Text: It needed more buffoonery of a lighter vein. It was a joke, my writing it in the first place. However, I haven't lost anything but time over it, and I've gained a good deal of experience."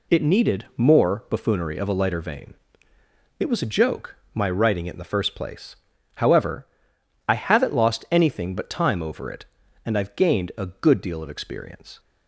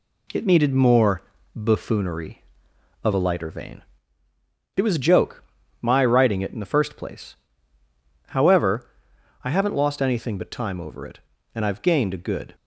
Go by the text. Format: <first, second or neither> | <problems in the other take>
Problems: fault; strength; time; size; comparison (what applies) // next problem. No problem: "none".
first | pauses between "more" and "buffoonery"; slight; at 1.2 s; 0.34 s long // stops before "deal of experience"; at 12.5 s